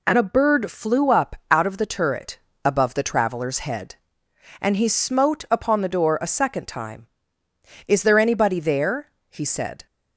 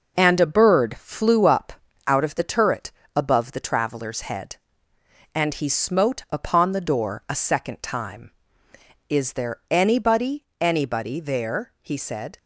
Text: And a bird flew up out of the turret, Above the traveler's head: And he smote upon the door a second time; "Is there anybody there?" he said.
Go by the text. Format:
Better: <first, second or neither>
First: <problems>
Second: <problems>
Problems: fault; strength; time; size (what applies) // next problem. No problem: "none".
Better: first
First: none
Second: pauses between "up" and "out"; slight; at 1.7 s; 0.34 s long // says "anybody" twice; at 10.6 s